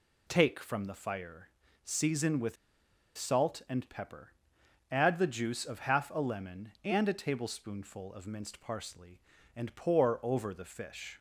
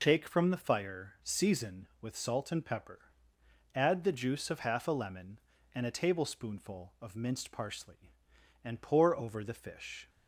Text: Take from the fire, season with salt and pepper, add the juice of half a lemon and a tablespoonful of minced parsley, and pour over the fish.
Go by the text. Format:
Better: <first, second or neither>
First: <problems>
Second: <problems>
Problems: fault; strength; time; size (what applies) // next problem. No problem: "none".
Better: second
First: pauses between "with" and "salt"; noticeable; at 2.5 s; 0.62 s long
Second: none